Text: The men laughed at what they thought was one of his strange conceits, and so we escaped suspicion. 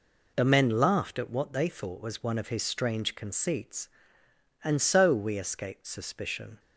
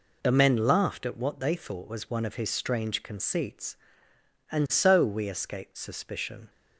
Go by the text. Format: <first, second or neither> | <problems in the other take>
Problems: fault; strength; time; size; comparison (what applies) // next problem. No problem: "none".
neither | none